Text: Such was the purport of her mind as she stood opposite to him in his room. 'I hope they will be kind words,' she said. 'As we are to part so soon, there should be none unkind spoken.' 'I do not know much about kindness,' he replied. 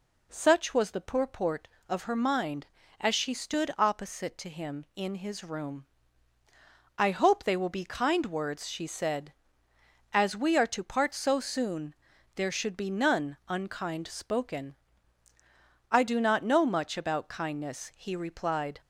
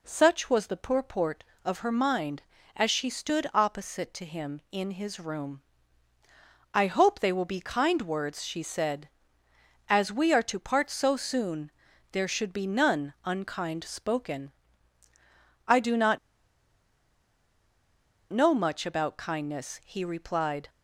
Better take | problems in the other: first | pauses between "not" and "know"; strong; at 16.1 s; 2.1 s long

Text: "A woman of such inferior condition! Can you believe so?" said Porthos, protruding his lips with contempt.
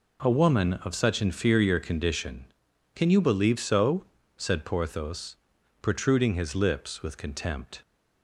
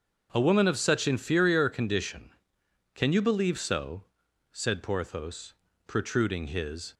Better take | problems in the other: first | starts louder than the rest; until 1.3 s; 6.5 dB // stops before "lips with contempt"; at 6.9 s

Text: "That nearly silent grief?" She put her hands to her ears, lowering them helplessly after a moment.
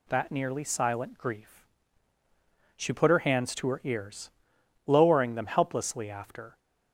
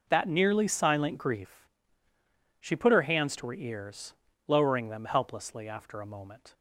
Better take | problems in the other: second | stops before "a moment"; at 6.5 s

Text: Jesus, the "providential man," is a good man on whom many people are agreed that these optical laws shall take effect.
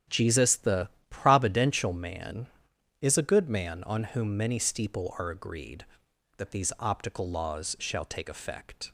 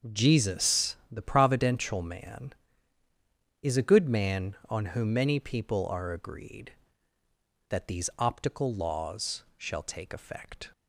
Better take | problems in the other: second | starts louder than the rest; strong; until 1.3 s; 10 dB; also in the second // pauses between "the" and "providential"; slight; at 0.8 s; 0.22 s long // says "steeple" for "people"; at 4.5 s

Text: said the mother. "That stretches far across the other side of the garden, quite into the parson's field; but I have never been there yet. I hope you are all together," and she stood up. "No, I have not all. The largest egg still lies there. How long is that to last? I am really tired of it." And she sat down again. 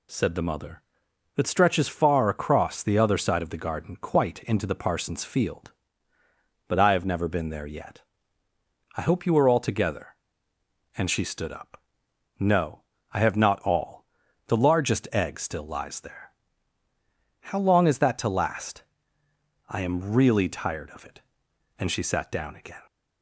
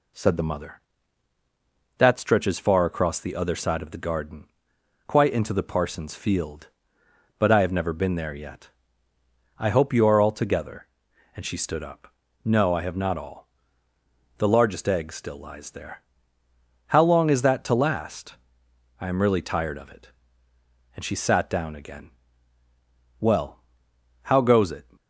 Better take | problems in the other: first | goes on to say "Well how goes it"; from 23.2 s on; 1.6 s long

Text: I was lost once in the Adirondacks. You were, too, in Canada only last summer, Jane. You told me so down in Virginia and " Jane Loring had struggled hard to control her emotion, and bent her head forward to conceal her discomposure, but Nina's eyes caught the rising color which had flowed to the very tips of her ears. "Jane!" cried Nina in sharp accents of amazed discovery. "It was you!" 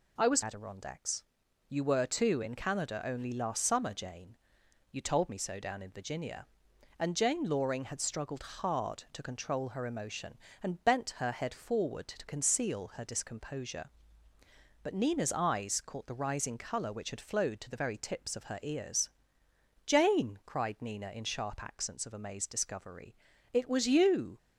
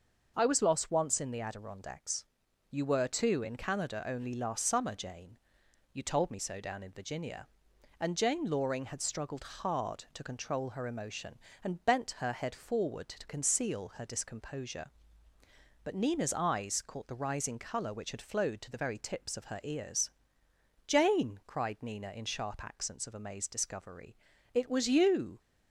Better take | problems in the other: second | skips "lost once in the"; at 0.4 s

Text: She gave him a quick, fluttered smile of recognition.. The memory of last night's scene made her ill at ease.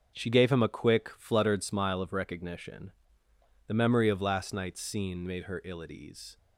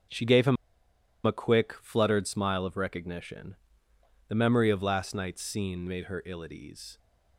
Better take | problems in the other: first | starts louder than the rest; until 1.8 s; 6.5 dB; also in the first // pauses between "him" and "a"; noticeable; at 0.5 s; 0.70 s long

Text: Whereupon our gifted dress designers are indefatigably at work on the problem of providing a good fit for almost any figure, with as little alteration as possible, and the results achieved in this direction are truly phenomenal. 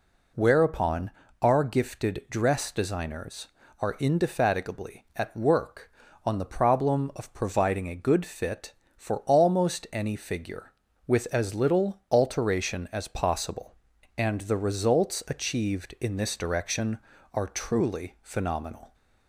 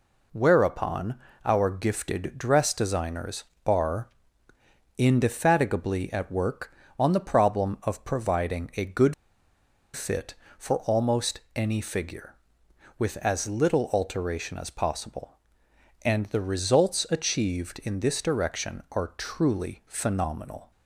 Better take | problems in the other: first | pauses between "Whereupon" and "our"; slight; at 1.1 s; 0.30 s long; slight in the first // pauses between "are" and "indefatigably"; noticeable; at 4.0 s; 0.90 s long // pauses between "good" and "fit"; noticeable; at 9.1 s; 0.82 s long // pauses between "almost" and "any"; slight; at 11.4 s; 0.16 s long

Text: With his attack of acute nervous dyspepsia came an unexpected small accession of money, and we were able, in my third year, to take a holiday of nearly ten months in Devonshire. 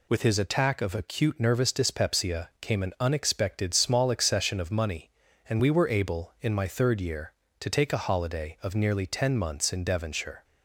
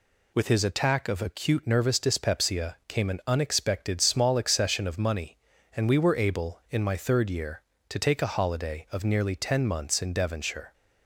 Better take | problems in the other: neither | none

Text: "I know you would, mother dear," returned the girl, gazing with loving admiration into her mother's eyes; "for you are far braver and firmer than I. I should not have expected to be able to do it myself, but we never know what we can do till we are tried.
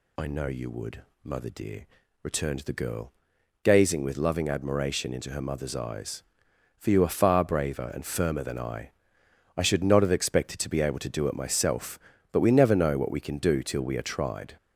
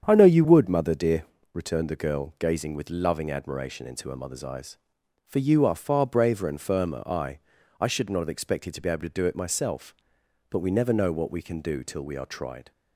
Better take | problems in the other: first | starts louder than the rest; strong; until 1.0 s; 8 dB // skips "than"; at 7.0 s

